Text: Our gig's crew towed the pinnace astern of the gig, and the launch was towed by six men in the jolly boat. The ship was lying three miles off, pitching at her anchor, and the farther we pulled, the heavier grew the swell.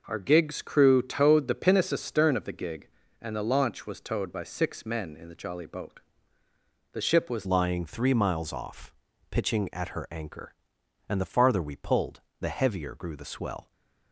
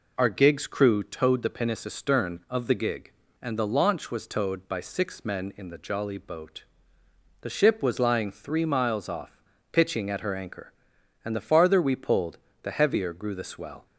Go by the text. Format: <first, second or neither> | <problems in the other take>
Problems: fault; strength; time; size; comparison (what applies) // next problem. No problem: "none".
second | changes voice at "lying"; from 7.4 s on; 6.3 s long